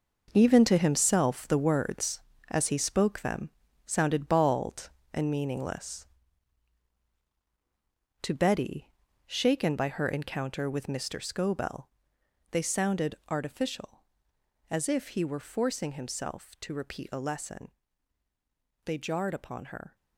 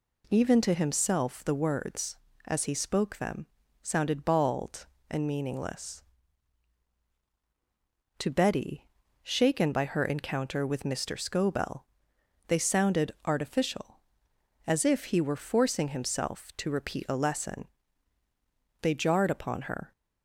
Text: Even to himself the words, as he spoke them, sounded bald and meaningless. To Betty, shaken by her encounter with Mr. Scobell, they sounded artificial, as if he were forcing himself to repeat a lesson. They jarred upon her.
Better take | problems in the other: second | gets quieter; strong; throughout; 10 dB

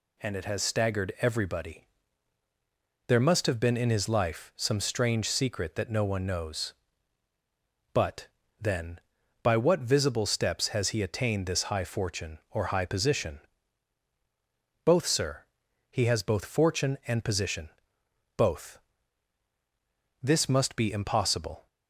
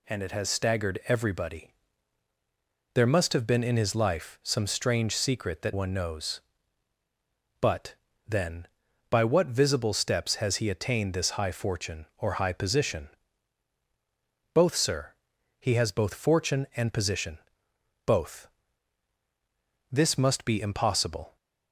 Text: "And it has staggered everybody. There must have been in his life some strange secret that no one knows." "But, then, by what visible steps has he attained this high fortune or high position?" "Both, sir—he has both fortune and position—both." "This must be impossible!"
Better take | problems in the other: first | skips "no"; at 5.7 s

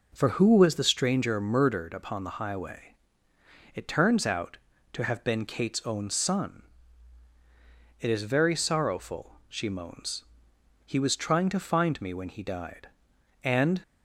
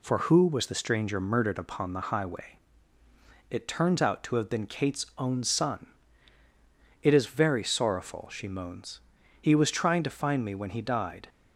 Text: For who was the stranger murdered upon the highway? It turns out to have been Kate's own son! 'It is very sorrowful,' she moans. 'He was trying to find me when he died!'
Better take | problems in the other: second | goes on to say "And"; slight; from 13.4 s on; 0.38 s long

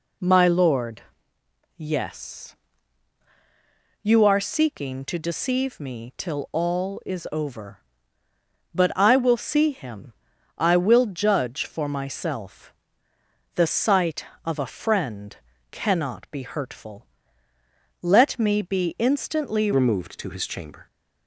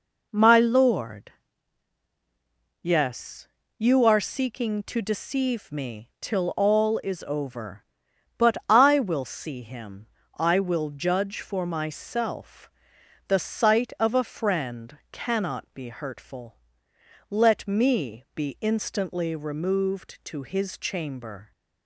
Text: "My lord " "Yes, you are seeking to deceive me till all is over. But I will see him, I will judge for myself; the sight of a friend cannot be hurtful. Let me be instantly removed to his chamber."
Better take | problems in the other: second | pauses between "friend" and "cannot"; slight; at 15.3 s; 0.34 s long // changes voice at "removed"; from 19.7 s on; 1.1 s long

